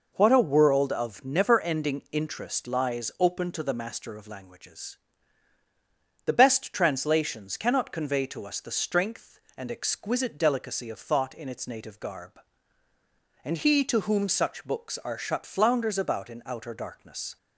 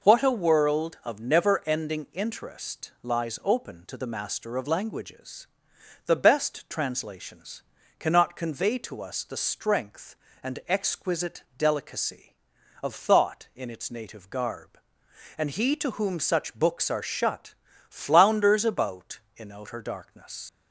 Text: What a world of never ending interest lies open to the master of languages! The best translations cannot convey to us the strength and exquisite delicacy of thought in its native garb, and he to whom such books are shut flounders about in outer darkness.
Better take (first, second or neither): first